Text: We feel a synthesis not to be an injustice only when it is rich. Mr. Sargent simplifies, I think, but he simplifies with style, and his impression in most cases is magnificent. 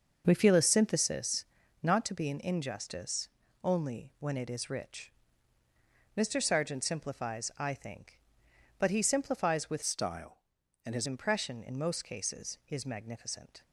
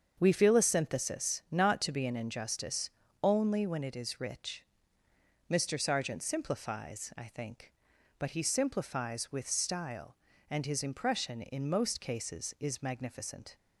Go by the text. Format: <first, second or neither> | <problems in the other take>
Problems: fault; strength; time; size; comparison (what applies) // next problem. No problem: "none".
second | starts louder than the rest; until 1.2 s; 6.5 dB; also in the second // pauses between "synthesis" and "not"; at 1.4 s; 0.40 s long // pauses between "injustice" and "only"; slight; at 3.2 s; 0.36 s long; slight in the second // changes voice from "style" to "his"; from 9.8 to 11.0 s; 1.2 s long